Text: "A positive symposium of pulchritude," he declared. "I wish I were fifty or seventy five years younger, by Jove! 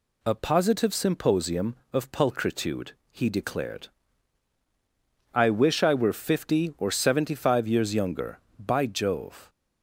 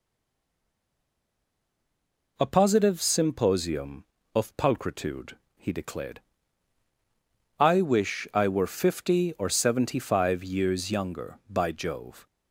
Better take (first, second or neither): first